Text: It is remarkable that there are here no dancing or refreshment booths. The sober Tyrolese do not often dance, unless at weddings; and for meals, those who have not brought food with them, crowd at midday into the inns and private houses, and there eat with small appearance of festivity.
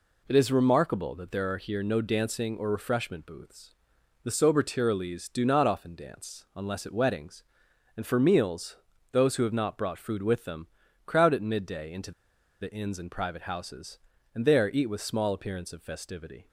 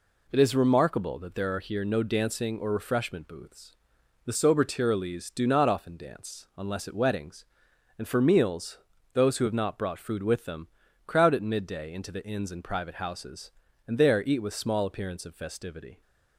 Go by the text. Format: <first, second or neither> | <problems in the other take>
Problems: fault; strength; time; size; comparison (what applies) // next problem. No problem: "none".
second | pauses between "into" and "the"; noticeable; at 12.1 s; 0.50 s long